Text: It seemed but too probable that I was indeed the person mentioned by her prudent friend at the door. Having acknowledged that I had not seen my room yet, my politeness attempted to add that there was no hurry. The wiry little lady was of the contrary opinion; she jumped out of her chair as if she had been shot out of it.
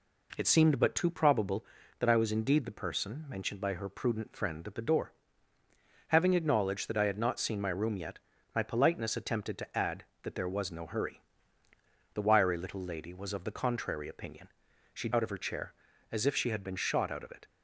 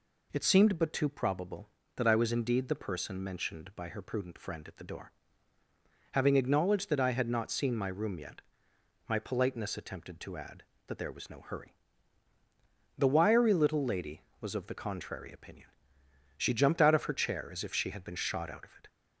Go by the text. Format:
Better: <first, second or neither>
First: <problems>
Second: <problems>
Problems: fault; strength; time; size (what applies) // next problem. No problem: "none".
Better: second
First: skips "jumped"; at 15.0 s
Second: none